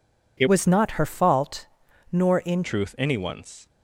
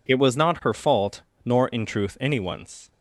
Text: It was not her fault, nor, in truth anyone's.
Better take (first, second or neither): second